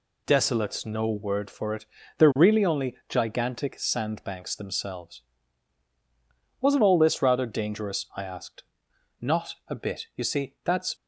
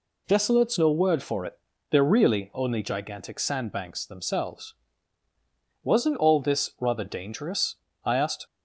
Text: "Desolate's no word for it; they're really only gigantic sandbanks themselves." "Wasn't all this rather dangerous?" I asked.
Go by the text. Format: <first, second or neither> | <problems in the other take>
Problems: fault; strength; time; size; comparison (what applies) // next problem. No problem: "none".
second | goes on to say "Not a bit you see that's"; strong; from 9.1 s on; 1.7 s long